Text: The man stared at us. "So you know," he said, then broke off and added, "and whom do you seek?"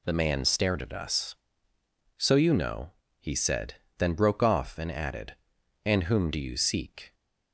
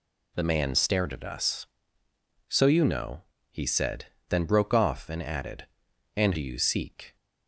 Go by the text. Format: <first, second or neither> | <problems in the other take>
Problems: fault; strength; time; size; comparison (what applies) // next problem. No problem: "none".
first | skips "whom"; at 6.3 s